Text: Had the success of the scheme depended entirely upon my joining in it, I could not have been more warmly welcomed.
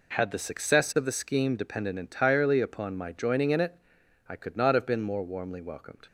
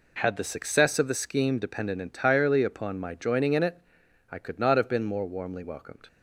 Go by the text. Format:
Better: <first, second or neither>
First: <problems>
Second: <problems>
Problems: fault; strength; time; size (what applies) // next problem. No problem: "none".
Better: neither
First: none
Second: none